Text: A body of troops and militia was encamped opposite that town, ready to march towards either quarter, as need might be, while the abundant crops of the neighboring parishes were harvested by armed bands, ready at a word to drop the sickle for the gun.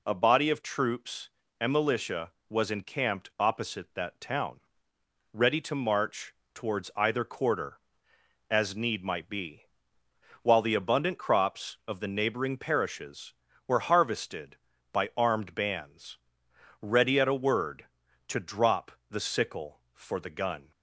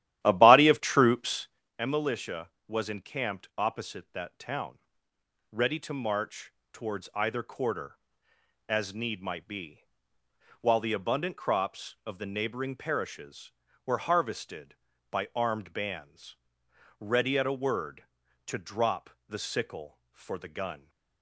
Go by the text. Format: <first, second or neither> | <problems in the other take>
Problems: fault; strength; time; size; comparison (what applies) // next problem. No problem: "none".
first | starts louder than the rest; strong; until 1.7 s; 13 dB // pauses between "march" and "towards"; slight; at 6.5 s; 0.22 s long; slight in the first // pauses between "drop" and "the"; slight; at 19.0 s; 0.20 s long; slight in the first